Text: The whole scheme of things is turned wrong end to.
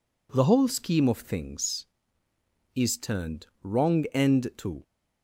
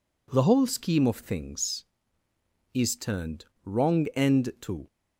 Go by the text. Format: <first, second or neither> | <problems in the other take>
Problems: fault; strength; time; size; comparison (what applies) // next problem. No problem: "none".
neither | pauses between "turned" and "wrong"; slight; the same in both